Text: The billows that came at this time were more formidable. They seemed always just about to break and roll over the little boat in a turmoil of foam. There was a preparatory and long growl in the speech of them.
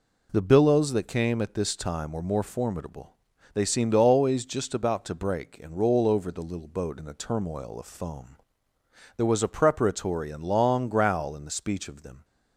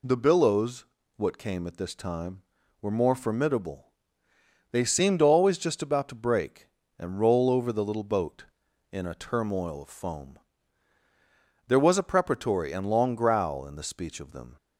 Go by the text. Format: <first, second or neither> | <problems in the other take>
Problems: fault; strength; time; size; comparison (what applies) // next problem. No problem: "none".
first | says "what" for "that"; at 1.1 s